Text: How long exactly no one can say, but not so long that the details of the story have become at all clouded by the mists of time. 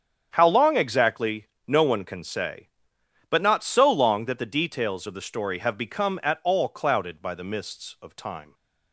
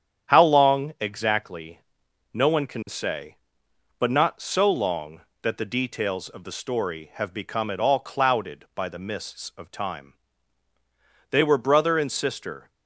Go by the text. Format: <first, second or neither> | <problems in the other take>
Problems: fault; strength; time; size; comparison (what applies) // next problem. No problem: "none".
first | starts louder than the rest; strong; until 1.3 s; 8.5 dB; strong in the first // pauses between "exactly" and "no"; noticeable; at 1.8 s; 0.50 s long; slight in the first // goes on to say "They were brother and sister"; from 11.2 s on; 1.4 s long